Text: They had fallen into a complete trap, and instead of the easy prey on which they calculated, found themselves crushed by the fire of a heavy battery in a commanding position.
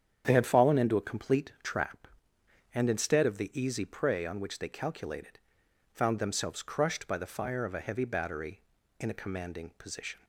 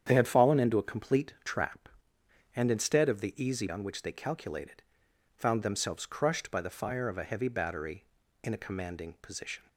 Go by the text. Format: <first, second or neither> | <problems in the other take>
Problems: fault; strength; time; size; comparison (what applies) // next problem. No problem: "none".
first | starts louder than the rest; strong; until 1.0 s; 8.5 dB; strong in the first // skips "prey"; at 3.6 s